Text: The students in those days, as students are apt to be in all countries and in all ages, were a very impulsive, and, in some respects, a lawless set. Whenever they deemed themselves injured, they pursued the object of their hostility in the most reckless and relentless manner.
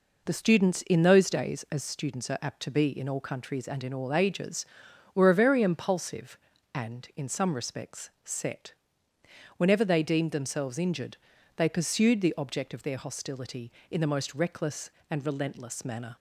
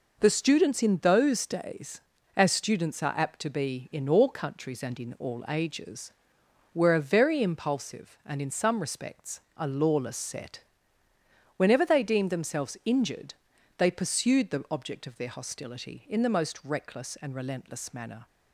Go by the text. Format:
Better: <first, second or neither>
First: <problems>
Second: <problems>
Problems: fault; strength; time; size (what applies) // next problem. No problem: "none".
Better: second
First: skips "a lawless"; at 8.1 s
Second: none